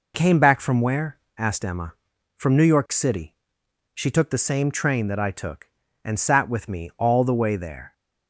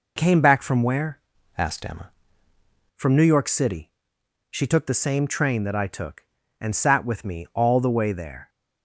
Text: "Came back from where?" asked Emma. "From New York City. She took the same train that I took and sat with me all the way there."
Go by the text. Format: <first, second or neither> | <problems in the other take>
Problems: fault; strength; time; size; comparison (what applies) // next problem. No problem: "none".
first | changes voice from "asked" to "Emma"; from 1.5 to 2.1 s; 0.6 s long